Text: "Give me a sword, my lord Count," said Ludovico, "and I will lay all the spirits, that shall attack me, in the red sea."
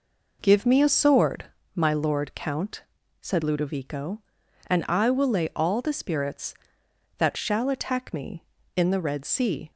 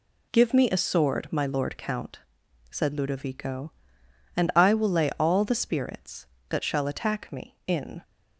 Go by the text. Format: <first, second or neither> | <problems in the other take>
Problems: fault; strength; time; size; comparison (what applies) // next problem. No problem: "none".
first | stops before "the red sea"; at 8.0 s